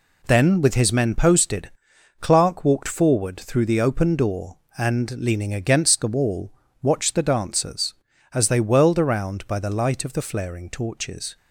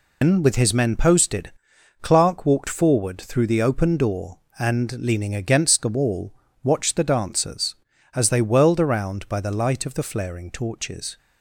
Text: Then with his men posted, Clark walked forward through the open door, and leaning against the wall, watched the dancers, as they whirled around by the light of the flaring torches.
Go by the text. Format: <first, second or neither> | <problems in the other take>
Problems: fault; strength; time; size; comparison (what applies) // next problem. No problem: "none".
first | loses the start of "Then"; at 0.2 s; 160 ms